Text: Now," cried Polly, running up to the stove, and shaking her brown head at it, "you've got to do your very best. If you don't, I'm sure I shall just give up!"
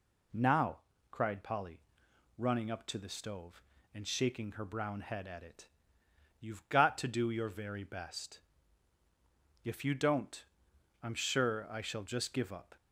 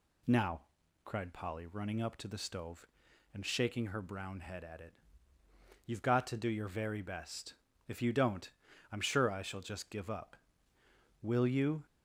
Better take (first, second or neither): first